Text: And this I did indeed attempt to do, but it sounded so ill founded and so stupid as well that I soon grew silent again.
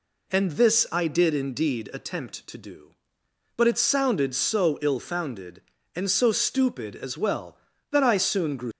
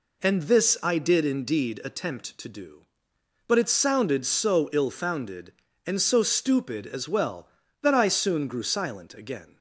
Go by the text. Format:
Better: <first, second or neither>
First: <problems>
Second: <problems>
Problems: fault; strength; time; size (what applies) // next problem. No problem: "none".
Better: second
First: stops before "silent again"; at 8.7 s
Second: none